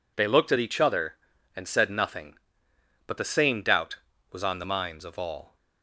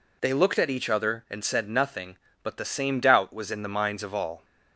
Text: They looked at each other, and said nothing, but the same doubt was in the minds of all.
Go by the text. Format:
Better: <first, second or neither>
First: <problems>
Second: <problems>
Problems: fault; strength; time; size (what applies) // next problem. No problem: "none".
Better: second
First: says "on" for "in"; at 4.4 s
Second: none